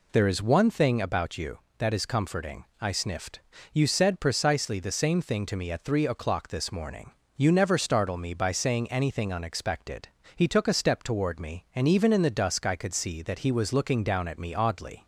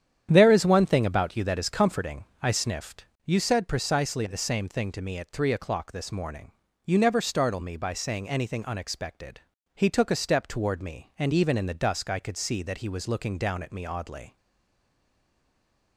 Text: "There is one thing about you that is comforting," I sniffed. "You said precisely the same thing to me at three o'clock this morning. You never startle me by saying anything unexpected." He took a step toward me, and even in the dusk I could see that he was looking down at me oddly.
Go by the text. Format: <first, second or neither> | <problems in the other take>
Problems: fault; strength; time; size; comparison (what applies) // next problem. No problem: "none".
first | starts louder than the rest; strong; until 1.3 s; 9.5 dB // stays silent after the last word; noticeable; from 14.3 s on; 1.6 s long